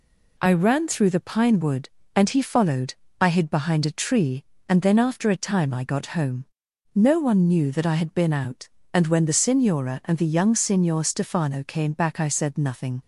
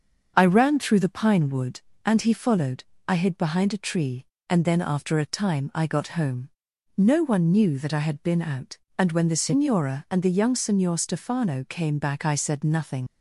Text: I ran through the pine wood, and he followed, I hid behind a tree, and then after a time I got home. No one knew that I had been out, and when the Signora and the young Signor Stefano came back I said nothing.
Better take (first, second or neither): first